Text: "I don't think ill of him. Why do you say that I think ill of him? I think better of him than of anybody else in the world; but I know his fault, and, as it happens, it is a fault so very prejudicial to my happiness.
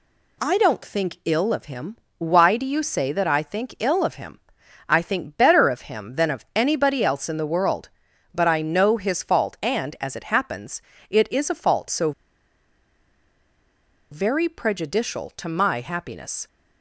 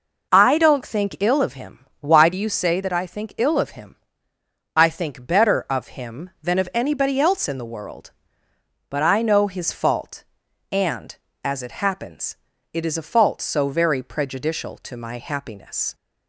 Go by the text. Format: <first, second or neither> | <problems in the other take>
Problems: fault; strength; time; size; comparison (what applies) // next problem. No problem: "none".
second | pauses between "so" and "very"; strong; at 12.1 s; 2.0 s long